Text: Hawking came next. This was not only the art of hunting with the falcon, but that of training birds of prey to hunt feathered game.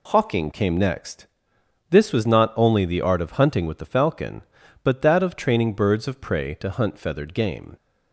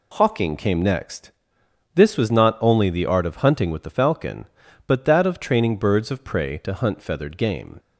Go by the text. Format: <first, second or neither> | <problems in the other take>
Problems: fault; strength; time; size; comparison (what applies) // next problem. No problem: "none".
neither | none